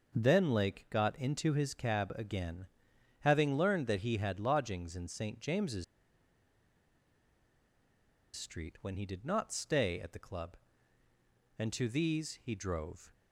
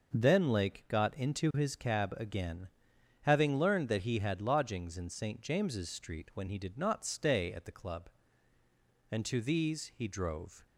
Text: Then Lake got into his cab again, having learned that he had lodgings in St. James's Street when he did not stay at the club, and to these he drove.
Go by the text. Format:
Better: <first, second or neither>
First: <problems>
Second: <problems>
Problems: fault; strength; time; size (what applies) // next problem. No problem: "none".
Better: second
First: pauses between "James's" and "Street"; strong; at 5.8 s; 2.5 s long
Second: none